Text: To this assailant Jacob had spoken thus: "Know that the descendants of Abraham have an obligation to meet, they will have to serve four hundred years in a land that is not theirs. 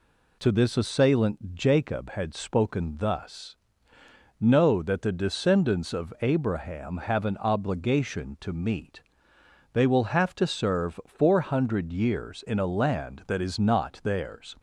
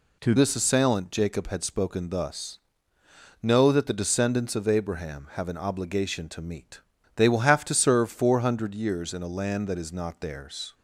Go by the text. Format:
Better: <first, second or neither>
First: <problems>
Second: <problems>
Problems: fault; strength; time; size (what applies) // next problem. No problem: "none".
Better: first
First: none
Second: changes voice at "this"; from 0.3 s on; 10.4 s long